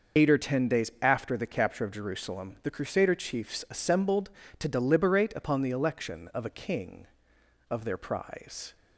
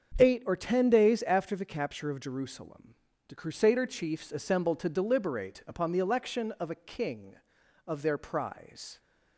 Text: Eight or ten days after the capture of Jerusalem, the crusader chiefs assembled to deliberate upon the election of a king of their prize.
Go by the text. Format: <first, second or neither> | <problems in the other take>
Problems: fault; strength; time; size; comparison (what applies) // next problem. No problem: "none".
second | loses the start of "Eight"; at 0.1 s; 85 ms // starts louder than the rest; until 1.2 s; 6 dB; also in the second